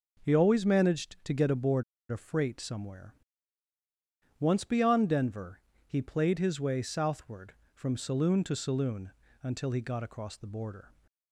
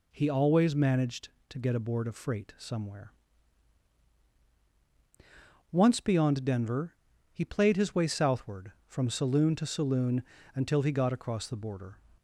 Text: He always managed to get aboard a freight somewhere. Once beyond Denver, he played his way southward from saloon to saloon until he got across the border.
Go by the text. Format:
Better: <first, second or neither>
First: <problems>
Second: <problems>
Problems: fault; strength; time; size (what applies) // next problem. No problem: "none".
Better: second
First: pauses between "aboard" and "a"; slight; at 1.8 s; 0.28 s long // pauses between "saloon" and "until"; slight; at 9.0 s; 0.32 s long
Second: pauses between "saloon" and "until"; slight; at 10.2 s; 0.32 s long